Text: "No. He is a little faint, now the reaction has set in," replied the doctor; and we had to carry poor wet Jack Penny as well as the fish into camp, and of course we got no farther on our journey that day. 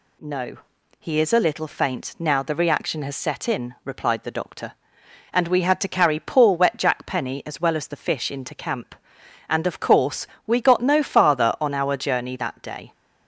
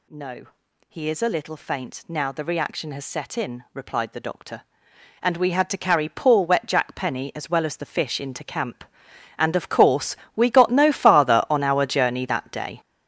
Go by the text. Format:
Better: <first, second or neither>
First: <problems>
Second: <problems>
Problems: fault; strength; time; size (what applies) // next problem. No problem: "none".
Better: first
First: pauses between "course" and "we"; slight; at 10.2 s; 0.18 s long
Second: gets louder; strong; throughout; 11.5 dB // pauses between "course" and "we"; slight; at 10.1 s; 0.18 s long